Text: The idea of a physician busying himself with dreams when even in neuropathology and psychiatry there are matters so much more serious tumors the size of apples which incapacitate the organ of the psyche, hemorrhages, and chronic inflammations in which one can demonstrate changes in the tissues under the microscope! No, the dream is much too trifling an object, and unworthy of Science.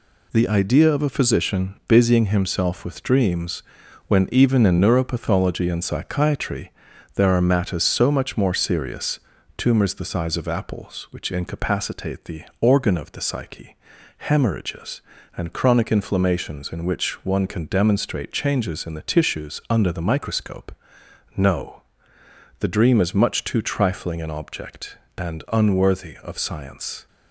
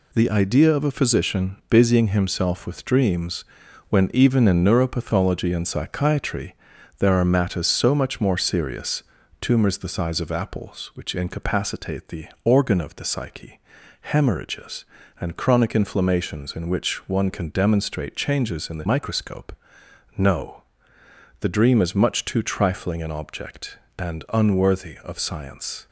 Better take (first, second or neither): first